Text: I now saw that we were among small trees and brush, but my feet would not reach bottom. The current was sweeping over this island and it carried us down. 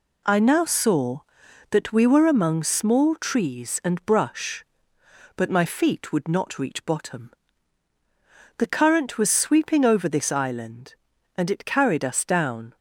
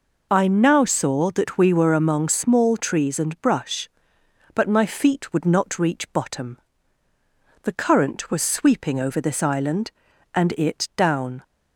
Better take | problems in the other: first | skips "carried us"; at 10.9 s

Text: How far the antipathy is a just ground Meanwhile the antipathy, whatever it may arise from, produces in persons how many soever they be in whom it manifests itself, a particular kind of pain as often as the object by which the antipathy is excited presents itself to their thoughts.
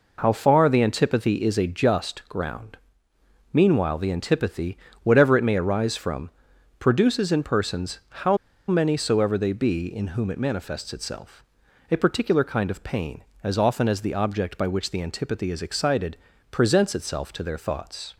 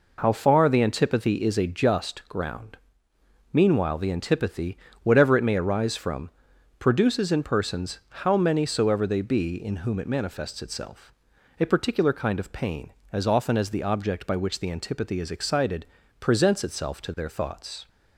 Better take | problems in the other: second | pauses between "ground" and "Meanwhile"; noticeable; at 2.7 s; 0.78 s long; noticeable in the second // pauses between "how" and "many"; slight; at 8.3 s; 0.33 s long // pauses between "excited" and "presents"; slight; at 16.1 s; 0.34 s long; slight in the second

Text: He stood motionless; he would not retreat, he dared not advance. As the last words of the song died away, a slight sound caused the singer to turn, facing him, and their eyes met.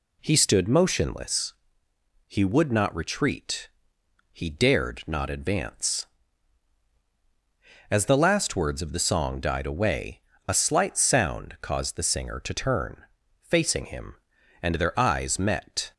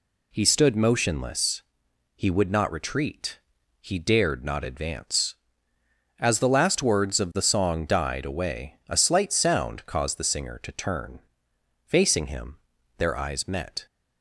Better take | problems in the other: first | skips "and"; at 12.7 s

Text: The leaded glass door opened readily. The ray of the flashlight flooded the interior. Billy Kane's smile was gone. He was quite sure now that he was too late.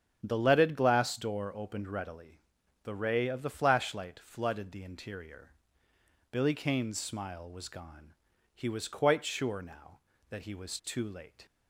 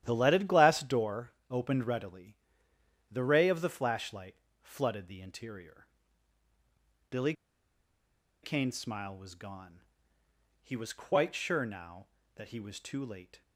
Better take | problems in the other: first | starts louder than the rest; strong; until 1.0 s; 11.5 dB; strong in the first // pauses between "door" and "opened"; slight; at 1.3 s; 0.16 s long // pauses between "flashlight" and "flooded"; slight; at 4.3 s; 0.26 s long // pauses between "Billy" and "Kane's"; at 7.3 s; 1.1 s long

